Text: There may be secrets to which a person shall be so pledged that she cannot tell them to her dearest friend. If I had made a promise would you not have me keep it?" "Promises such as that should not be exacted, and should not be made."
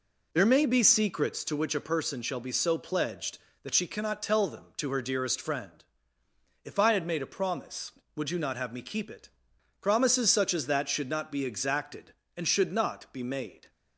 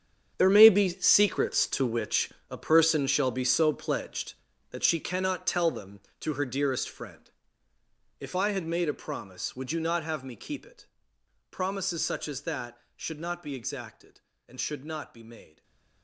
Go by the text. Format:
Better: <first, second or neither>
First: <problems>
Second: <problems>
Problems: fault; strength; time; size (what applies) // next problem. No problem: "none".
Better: first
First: none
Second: gets quieter; strong; throughout; 14 dB // pauses between "which" and "a"; slight; at 2.3 s; 0.20 s long // stays silent after the last word; slight; from 15.4 s on; 0.6 s long